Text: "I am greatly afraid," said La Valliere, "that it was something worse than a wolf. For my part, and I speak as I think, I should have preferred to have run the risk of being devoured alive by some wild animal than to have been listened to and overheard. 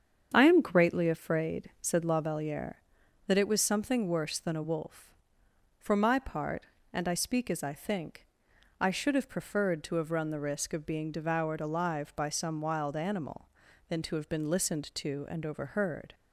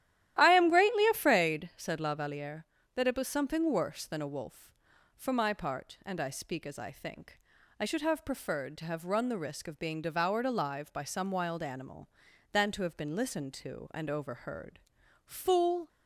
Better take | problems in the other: first | starts louder than the rest; strong; until 1.3 s; 12.5 dB; strong in the first // goes on to say "Fool"; noticeable; from 15.2 s on; 0.62 s long

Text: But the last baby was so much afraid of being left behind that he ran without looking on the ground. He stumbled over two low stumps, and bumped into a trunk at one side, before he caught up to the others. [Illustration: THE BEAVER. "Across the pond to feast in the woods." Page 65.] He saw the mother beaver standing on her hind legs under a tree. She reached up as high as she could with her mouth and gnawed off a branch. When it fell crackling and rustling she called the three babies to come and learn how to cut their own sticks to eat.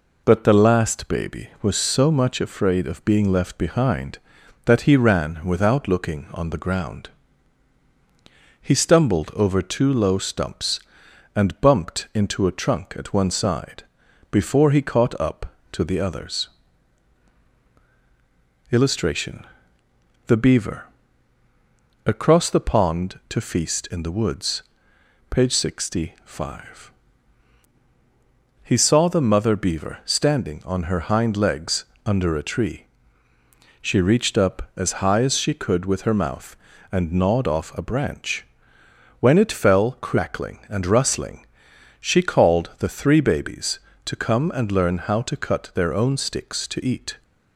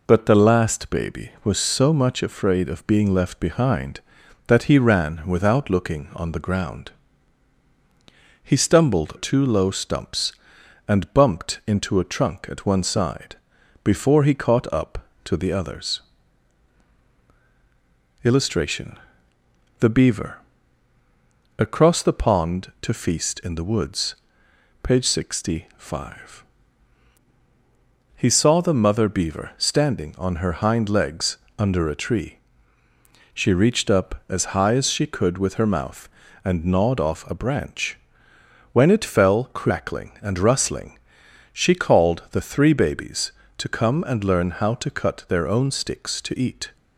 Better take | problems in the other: first | skips "over"; at 9.1 s // pauses between "legs" and "under"; slight; at 31.3 s; 0.22 s long; slight in the first // pauses between "rustling" and "she"; noticeable; at 40.9 s; 0.56 s long; noticeable in the first

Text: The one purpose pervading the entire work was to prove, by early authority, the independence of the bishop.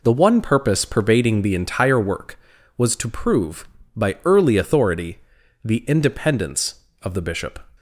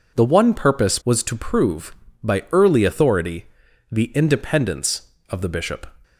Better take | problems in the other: first | skips "pervading the entire work"; at 1.0 s

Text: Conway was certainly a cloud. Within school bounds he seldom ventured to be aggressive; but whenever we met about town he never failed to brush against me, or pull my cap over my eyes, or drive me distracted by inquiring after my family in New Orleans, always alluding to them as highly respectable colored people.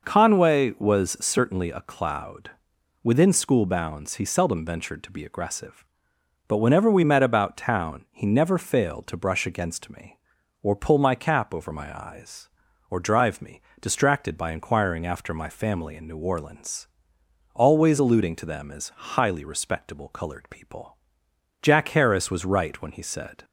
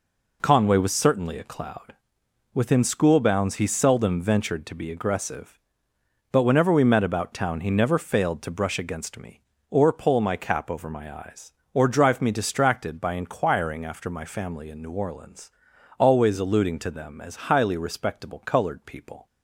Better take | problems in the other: second | pauses between "me" and "distracted"; slight; at 13.6 s; 0.18 s long // goes on to say "Jack Harris was right when he said"; strong; from 21.6 s on; 1.8 s long

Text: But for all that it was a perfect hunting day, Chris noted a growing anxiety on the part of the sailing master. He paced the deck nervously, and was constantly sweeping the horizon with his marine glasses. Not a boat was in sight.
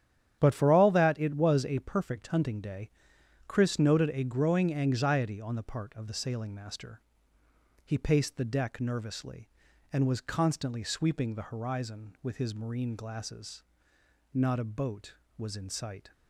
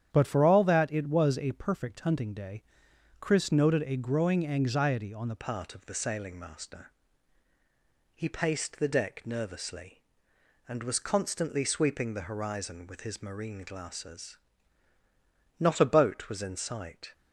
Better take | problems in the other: first | starts louder than the rest; strong; until 1.1 s; 9.5 dB; strong in the first // changes voice at "part"; from 5.3 s on; 11.8 s long

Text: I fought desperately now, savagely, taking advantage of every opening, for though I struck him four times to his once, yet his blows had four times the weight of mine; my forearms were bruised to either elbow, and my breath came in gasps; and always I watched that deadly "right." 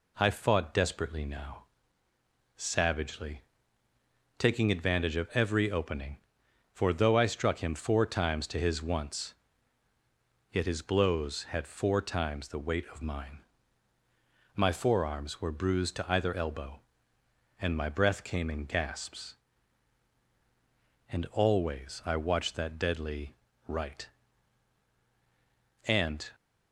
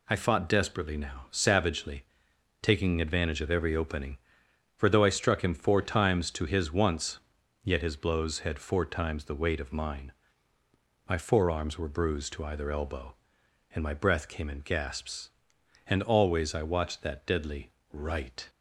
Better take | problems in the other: second | pauses between "deadly" and "right"; slight; at 23.3 s; 0.32 s long; slight in the second // goes on to say "And"; slight; from 25.8 s on; 0.42 s long

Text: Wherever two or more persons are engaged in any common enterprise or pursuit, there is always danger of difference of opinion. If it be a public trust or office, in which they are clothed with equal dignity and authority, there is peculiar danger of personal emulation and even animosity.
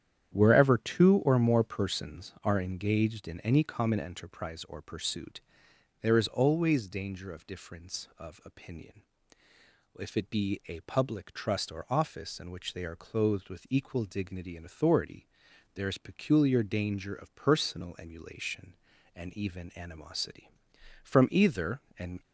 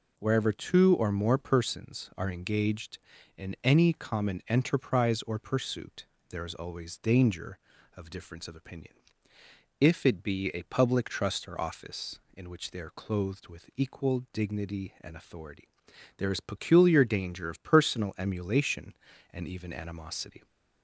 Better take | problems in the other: second | starts louder than the rest; strong; until 1.3 s; 9.5 dB // goes on to say "From either and"; noticeable; from 21.0 s on; 1.2 s long

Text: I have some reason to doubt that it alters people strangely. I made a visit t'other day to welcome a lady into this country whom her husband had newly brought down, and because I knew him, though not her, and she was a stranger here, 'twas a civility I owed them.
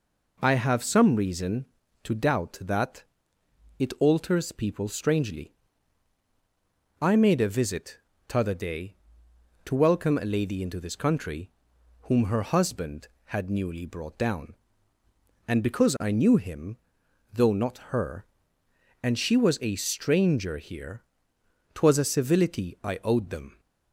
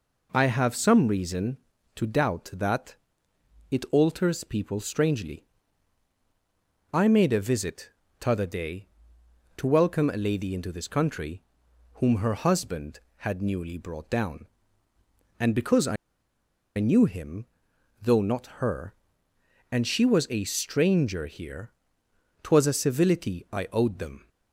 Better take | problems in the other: first | pauses between "that" and "it"; noticeable; at 2.9 s; 0.74 s long; noticeable in the first // pauses between "visit" and "t'other"; slight; at 7.8 s; 0.32 s long; slight in the first // pauses between "country" and "whom"; noticeable; at 11.4 s; 0.54 s long; noticeable in the first // pauses between "I" and "knew"; noticeable; at 15.9 s; 0.82 s long

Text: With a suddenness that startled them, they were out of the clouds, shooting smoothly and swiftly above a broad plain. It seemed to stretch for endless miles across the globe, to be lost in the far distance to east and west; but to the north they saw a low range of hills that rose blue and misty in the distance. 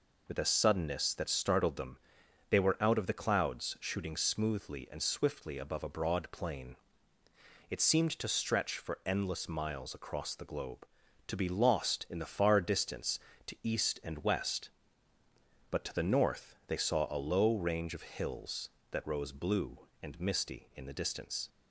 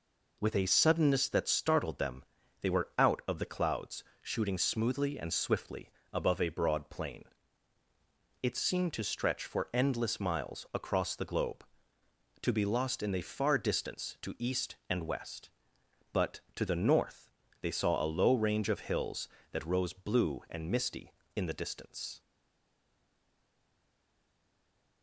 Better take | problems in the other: first | pauses between "swiftly" and "above"; slight; at 5.8 s; 0.22 s long // pauses between "north" and "they"; slight; at 17.3 s; 0.30 s long // stays silent after the last word; strong; from 22.1 s on; 2.9 s long

